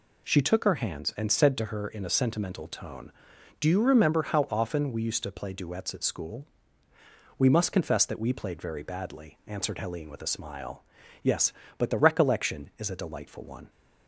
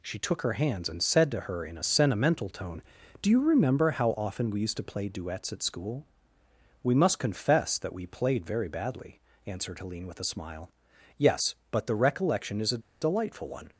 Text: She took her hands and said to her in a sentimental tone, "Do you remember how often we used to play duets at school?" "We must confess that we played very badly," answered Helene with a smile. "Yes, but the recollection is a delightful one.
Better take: first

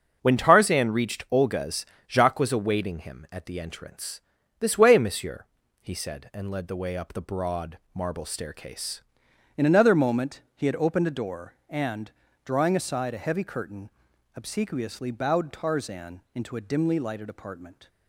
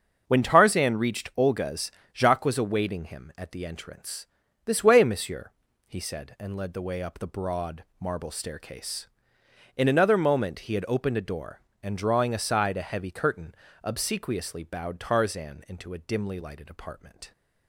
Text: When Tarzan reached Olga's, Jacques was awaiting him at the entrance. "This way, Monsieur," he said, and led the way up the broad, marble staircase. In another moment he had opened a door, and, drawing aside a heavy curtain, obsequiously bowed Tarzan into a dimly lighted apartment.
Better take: second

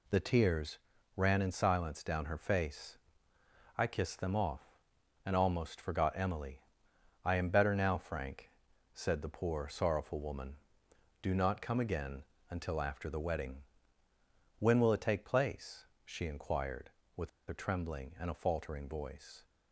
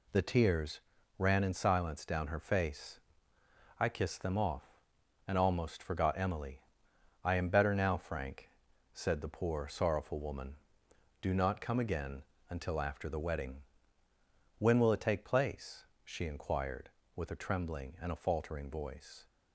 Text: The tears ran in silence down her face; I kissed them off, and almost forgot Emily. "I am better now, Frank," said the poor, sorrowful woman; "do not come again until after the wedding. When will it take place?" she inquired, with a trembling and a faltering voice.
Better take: second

